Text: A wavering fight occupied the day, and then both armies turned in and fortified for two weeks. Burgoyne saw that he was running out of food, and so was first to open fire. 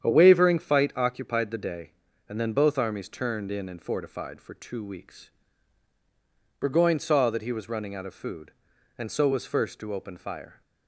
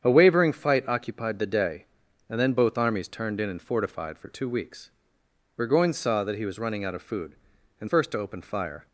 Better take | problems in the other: first | starts louder than the rest; strong; until 1.0 s; 8 dB; strong in the first // skips "so was"; at 7.8 s

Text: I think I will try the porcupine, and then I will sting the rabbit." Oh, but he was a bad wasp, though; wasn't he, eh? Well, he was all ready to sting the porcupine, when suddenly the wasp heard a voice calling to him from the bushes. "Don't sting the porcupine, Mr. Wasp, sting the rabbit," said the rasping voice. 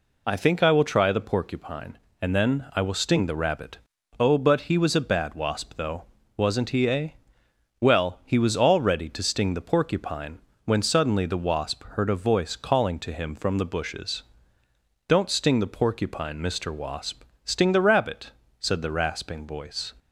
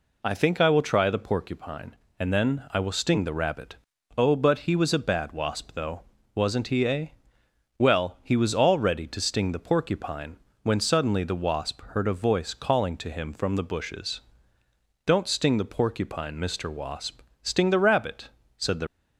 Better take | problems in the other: first | stops before "rasping voice"; at 18.8 s

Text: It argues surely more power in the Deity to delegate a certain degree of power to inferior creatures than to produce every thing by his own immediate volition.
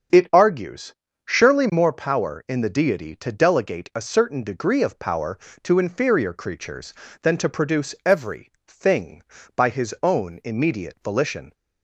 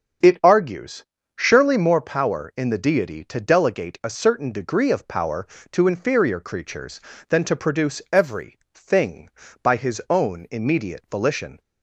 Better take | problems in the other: neither | starts louder than the rest; the same in both // pauses between "argues" and "surely"; slight; the same in both // pauses between "every" and "thing"; slight; the same in both

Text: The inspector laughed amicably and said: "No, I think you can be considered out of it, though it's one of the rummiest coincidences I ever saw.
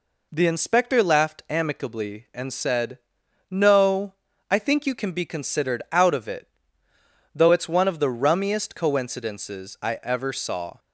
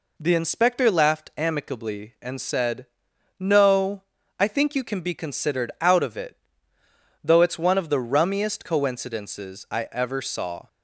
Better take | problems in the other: neither | none

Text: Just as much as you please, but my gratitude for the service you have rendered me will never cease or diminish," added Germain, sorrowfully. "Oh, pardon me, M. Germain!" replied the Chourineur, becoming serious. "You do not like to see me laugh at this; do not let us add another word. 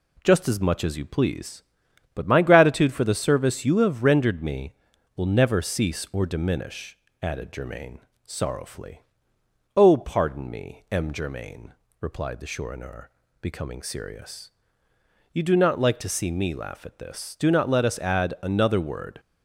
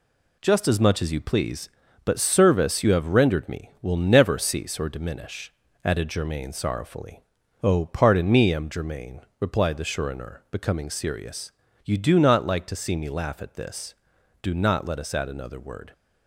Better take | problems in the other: first | skips "my gratitude for the"; at 2.2 s

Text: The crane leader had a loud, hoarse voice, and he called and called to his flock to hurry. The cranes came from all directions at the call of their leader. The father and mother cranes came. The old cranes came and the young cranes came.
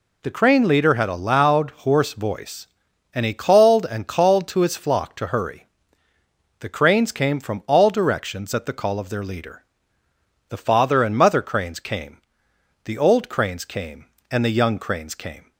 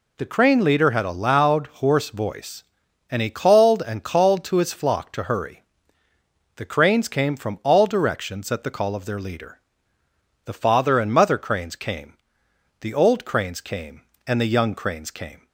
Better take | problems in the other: neither | none

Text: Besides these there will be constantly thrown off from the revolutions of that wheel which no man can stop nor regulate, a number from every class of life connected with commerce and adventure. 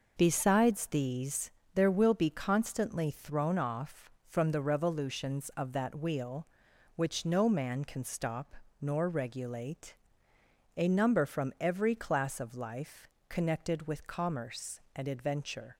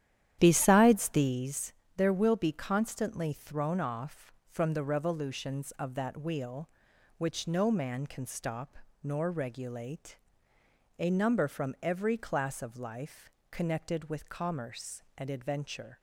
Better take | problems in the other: first | starts louder than the rest; strong; until 1.5 s; 11 dB // pauses between "these" and "there"; slight; at 1.7 s; 0.24 s long; slight in the first // pauses between "stop" and "nor"; slight; at 8.7 s; 0.26 s long; slight in the first // pauses between "life" and "connected"; slight; at 13.2 s; 0.20 s long; slight in the first

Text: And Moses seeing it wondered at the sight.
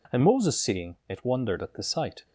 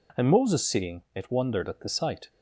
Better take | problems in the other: neither | none

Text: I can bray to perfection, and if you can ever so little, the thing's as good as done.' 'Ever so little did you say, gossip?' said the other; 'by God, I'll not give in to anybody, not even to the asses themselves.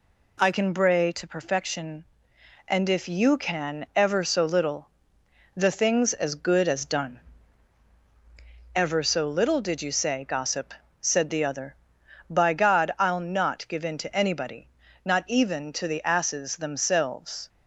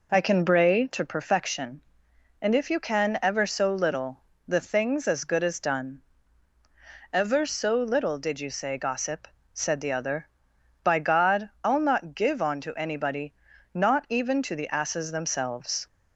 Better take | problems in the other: first | says "on" for "in"; at 12.4 s

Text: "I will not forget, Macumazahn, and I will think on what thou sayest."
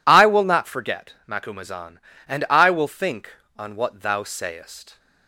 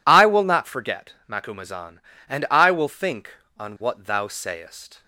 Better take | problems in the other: neither | none

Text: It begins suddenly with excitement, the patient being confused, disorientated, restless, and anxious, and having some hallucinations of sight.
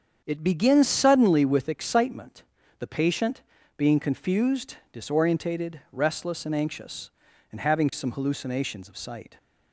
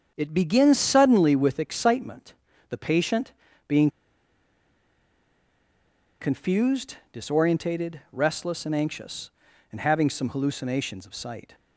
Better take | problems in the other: first | starts louder than the rest; strong; until 1.1 s; 7.5 dB; strong in the first // pauses between "patient" and "being"; slight; at 3.3 s; 0.36 s long; slight in the first // pauses between "being" and "confused"; strong; at 3.8 s; 2.3 s long

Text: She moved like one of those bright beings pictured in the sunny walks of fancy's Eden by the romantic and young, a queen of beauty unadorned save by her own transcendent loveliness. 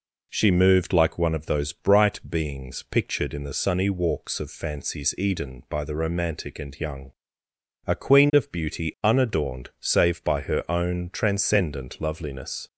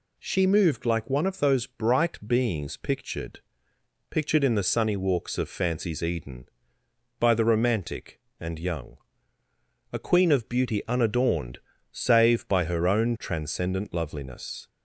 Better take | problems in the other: first | says "pictured" twice; at 4.0 s // pauses between "unadorned" and "save"; slight; at 11.5 s; 0.32 s long

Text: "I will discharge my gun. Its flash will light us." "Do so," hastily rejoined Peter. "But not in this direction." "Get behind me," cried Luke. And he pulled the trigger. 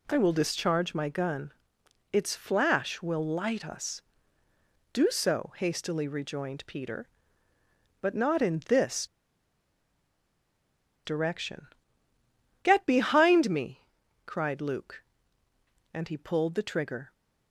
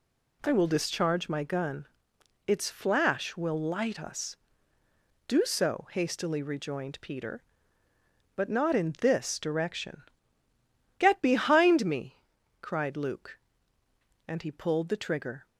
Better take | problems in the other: second | pauses between "this" and "direction"; strong; at 9.0 s; 1.9 s long

